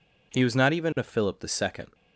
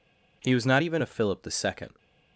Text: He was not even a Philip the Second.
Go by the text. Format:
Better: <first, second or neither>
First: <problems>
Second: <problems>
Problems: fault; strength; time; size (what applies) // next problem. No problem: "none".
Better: neither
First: none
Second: none